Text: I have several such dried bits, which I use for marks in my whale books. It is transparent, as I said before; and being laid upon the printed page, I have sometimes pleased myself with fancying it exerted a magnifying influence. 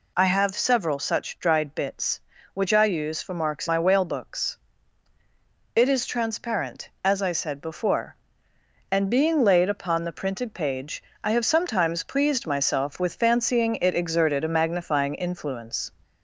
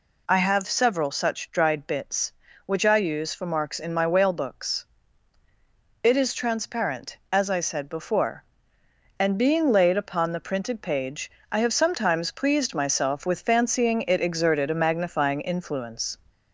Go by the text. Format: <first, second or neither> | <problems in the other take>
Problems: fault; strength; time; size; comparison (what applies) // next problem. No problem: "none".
second | skips "in"; at 3.6 s